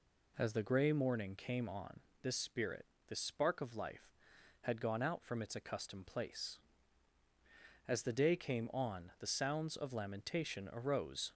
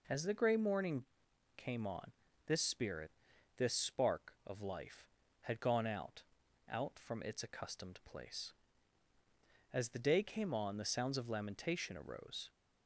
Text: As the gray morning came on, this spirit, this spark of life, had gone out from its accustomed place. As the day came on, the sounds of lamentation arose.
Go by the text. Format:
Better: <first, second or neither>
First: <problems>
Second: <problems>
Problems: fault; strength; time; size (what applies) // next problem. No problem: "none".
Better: first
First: none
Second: pauses between "morning" and "came"; noticeable; at 1.0 s; 0.52 s long // says "out" twice; at 6.6 s